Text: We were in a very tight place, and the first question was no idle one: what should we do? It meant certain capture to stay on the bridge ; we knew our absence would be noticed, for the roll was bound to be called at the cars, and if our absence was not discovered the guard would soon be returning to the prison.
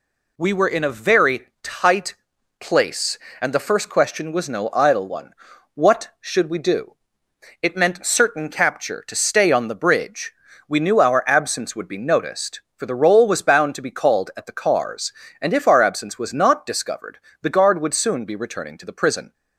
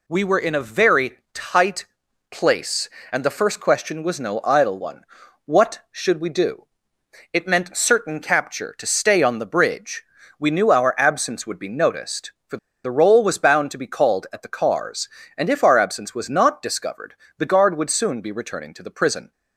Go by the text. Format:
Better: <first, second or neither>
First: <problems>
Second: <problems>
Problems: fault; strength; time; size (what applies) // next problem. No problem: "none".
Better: first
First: pauses between "tight" and "place"; noticeable; at 2.1 s; 0.46 s long // pauses between "discovered" and "the"; slight; at 17.1 s; 0.24 s long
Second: pauses between "tight" and "place"; noticeable; at 1.8 s; 0.46 s long // pauses between "for" and "the"; slight; at 12.5 s; 0.27 s long // pauses between "discovered" and "the"; slight; at 17.1 s; 0.24 s long